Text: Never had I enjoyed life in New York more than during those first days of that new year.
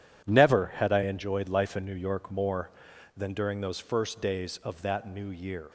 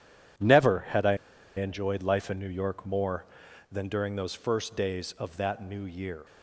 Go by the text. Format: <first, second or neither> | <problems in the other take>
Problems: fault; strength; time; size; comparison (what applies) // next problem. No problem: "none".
first | pauses between "I" and "enjoyed"; at 1.1 s; 0.40 s long